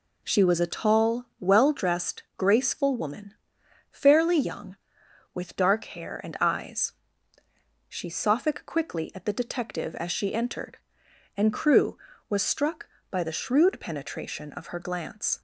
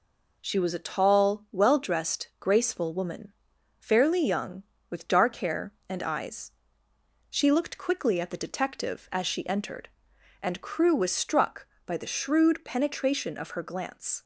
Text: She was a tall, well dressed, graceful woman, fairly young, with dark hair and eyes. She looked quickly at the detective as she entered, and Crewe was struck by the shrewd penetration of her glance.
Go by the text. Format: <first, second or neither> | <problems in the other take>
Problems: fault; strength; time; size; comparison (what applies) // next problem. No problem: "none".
second | says "sophic" for "looked"; at 8.0 s